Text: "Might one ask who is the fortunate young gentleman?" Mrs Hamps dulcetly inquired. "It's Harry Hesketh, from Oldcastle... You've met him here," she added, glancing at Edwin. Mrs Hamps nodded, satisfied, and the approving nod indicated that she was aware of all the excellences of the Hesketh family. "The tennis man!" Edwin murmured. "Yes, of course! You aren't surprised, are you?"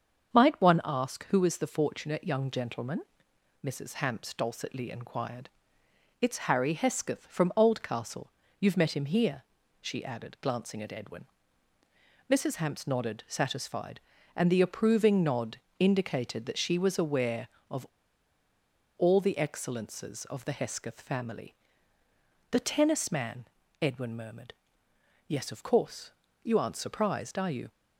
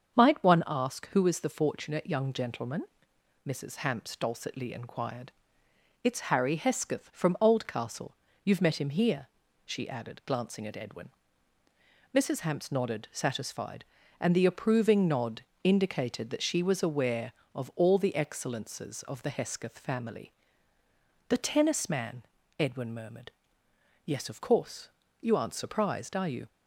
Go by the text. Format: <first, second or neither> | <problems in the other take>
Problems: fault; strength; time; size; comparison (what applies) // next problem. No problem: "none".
second | starts louder than the rest; until 1.4 s; 7 dB; also in the second // pauses between "nod" and "indicated"; slight; at 15.5 s; 0.22 s long; slight in the second // pauses between "of" and "all"; at 17.8 s; 1.1 s long